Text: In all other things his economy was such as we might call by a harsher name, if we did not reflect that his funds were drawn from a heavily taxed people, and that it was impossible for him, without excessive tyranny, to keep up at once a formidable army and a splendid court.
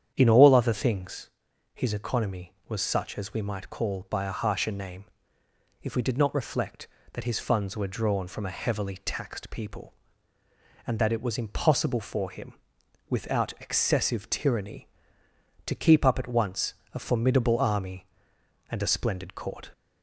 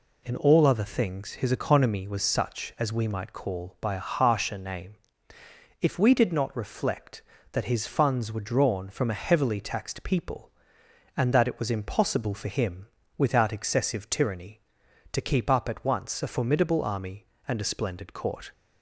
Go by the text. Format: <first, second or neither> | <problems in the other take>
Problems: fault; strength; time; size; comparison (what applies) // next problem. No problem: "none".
second | starts louder than the rest; strong; until 1.5 s; 9 dB // pauses between "things" and "his"; at 1.2 s; 0.44 s long // pauses between "once" and "a"; slight; at 16.7 s; 0.20 s long